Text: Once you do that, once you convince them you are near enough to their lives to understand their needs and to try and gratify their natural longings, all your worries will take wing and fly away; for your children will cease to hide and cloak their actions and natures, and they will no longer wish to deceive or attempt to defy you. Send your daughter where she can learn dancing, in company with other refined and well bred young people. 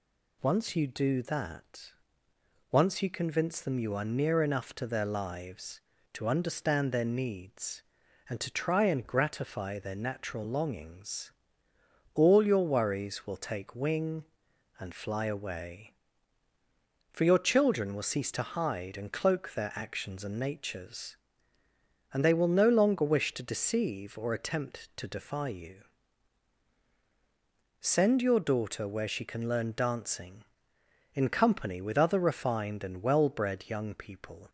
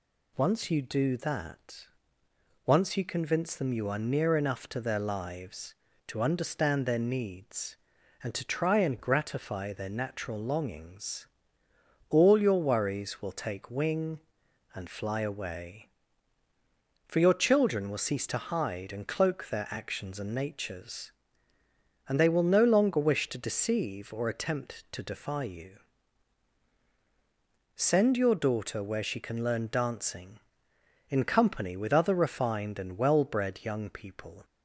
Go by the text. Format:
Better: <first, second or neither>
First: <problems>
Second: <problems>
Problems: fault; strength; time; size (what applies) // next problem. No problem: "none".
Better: neither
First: none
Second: none